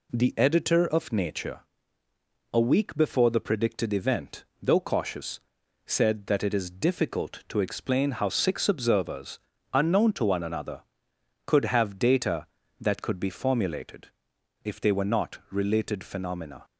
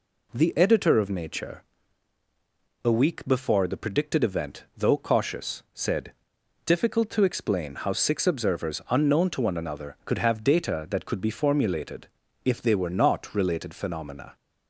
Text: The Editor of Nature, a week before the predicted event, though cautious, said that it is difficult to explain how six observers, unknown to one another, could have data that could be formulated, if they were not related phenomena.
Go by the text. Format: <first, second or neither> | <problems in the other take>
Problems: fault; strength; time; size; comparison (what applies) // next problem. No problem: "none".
first | skips "that it is"; at 6.4 s